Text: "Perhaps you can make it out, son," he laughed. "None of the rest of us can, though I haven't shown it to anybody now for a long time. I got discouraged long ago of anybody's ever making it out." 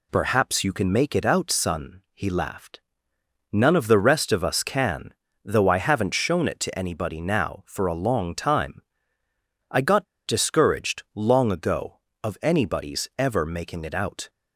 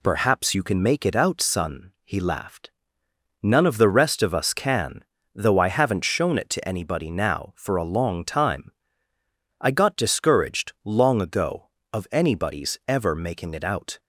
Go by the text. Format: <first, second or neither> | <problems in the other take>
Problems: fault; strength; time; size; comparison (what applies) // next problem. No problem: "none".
second | pauses between "got" and "discouraged"; slight; at 10.0 s; 0.21 s long